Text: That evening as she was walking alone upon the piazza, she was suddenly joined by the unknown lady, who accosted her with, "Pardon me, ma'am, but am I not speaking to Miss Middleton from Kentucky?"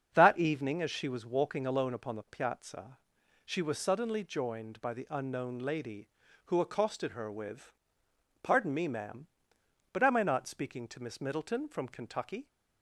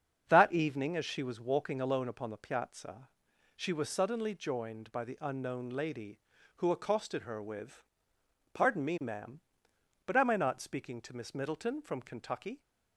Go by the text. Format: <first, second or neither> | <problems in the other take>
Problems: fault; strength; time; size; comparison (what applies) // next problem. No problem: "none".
neither | starts louder than the rest; the same in both